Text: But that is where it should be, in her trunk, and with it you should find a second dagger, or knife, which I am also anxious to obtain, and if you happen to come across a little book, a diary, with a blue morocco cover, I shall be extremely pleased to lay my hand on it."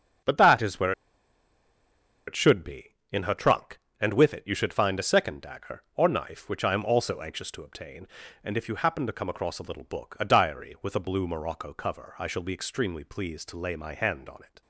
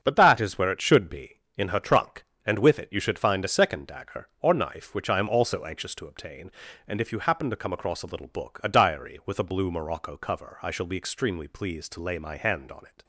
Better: second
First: starts louder than the rest; until 2.6 s; 7 dB // pauses between "where" and "it"; strong; at 0.9 s; 1.3 s long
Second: starts louder than the rest; until 1.0 s; 7 dB

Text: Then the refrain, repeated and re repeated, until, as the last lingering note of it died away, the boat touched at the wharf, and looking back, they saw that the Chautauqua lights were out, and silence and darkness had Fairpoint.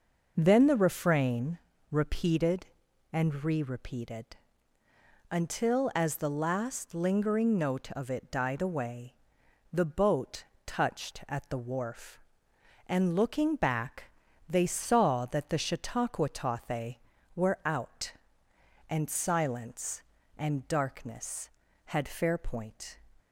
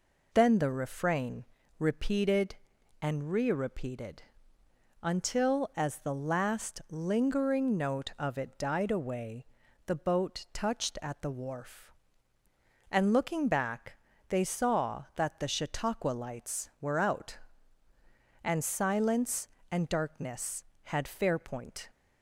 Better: second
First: pauses between "boat" and "touched"; slight; at 10.4 s; 0.22 s long // says "tothe" for "lights"; at 16.2 s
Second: none

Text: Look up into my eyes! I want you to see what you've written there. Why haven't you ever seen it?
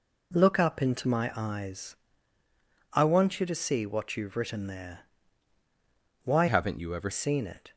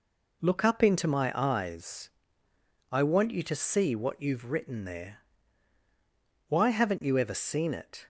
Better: second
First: changes voice from "haven't" to "ever"; from 6.4 to 7.1 s; 0.7 s long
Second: none

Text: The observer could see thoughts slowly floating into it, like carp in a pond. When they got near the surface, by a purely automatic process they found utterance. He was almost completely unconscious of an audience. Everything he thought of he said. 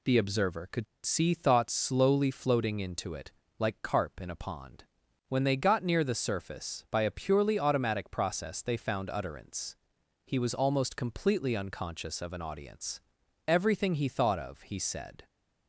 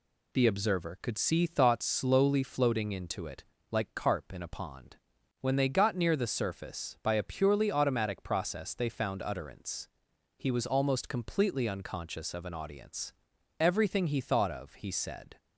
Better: second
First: pauses between "could" and "see"; slight; at 0.8 s; 0.20 s long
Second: none

